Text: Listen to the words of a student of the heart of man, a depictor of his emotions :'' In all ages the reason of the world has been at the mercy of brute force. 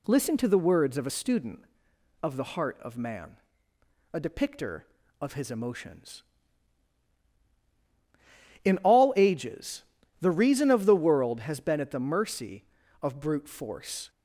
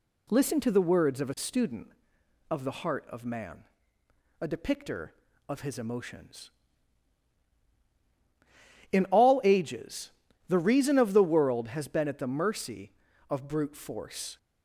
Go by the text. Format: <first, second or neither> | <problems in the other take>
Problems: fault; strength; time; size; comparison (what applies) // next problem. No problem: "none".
neither | pauses between "ages" and "the"; slight; the same in both